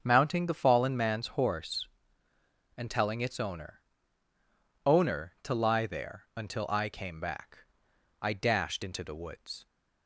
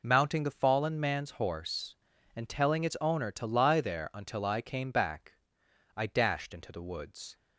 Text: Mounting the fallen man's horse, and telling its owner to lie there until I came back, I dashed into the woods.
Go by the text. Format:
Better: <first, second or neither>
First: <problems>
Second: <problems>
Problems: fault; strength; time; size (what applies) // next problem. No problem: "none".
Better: second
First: starts louder than the rest; until 1.0 s; 7 dB // says "owner" twice; at 4.8 s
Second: none